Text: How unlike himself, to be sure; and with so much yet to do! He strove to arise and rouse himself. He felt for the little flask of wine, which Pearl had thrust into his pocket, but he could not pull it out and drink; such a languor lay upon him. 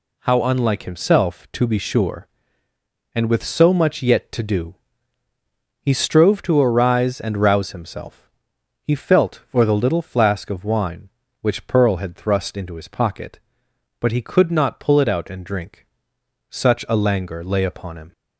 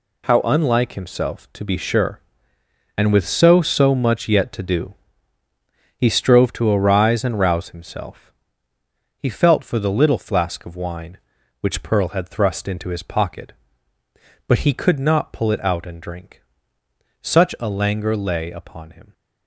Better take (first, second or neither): first